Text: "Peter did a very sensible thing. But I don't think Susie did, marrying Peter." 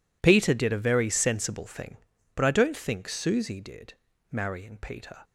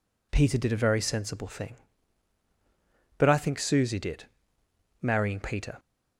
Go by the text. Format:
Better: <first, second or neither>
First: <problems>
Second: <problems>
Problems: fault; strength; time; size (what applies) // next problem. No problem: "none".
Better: first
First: none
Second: skips "don't"; at 3.3 s